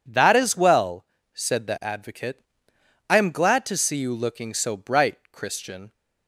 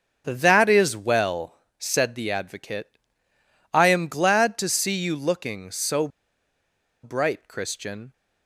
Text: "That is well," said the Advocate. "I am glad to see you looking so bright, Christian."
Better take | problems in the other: first | starts louder than the rest; until 1.2 s; 6.5 dB // pauses between "so" and "bright"; noticeable; at 6.0 s; 0.95 s long

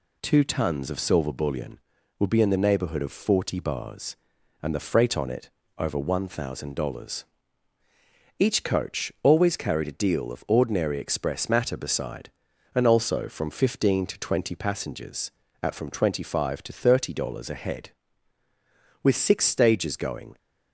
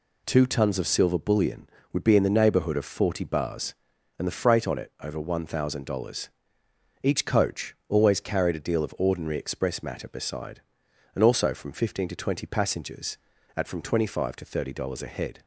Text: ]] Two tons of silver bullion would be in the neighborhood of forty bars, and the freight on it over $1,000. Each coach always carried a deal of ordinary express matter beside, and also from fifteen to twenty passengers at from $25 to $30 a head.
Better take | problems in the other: second | pauses between "it" and "over"; slight; at 5.4 s; 0.28 s long // goes on to say "With six stages going"; from 19.0 s on; 1.3 s long

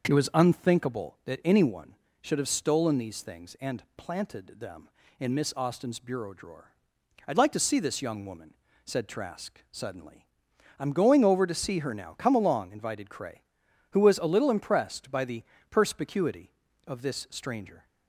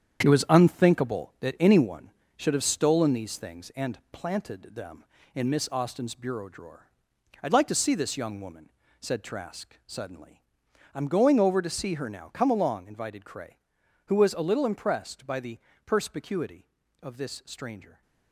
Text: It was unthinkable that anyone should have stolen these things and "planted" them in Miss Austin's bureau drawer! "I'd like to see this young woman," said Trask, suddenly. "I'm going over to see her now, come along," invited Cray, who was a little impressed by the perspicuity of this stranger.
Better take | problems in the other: first | gets quieter; strong; throughout; 7.5 dB // pauses between "the" and "perspicuity"; slight; at 15.5 s; 0.30 s long; slight in the first

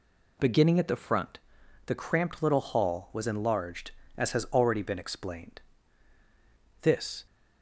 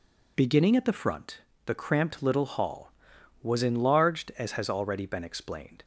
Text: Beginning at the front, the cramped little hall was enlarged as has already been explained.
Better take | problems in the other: second | goes on to say "This"; slight; from 6.8 s on; 0.42 s long

